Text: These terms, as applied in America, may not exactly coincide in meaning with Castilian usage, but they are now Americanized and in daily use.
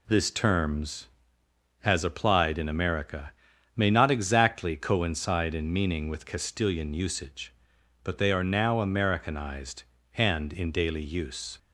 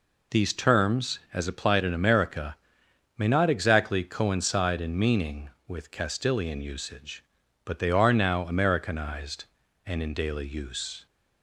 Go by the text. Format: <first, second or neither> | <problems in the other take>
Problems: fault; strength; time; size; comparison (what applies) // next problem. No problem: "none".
second | says "This" for "These"; at 0.0 s